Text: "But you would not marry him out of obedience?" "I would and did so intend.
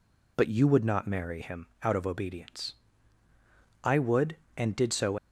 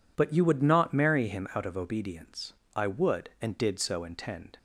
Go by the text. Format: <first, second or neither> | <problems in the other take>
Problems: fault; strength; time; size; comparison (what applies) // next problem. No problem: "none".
second | stops before "intend"; at 5.1 s